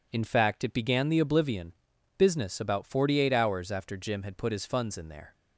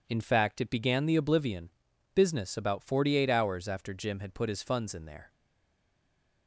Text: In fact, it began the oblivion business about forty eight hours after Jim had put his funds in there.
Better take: first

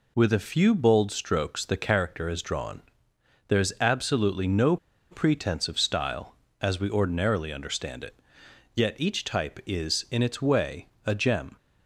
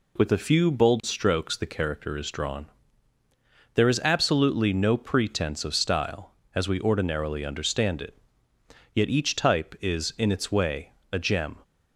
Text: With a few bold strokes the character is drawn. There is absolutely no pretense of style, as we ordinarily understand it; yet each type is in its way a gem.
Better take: second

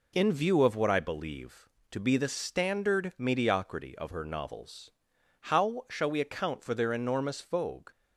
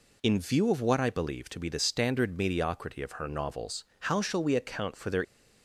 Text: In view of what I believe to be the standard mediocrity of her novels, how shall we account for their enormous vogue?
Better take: first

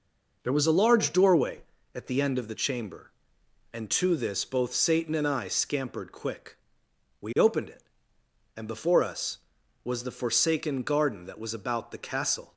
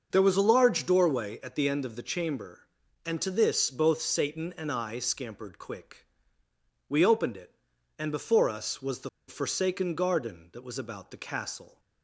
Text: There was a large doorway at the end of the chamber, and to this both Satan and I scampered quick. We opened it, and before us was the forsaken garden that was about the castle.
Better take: first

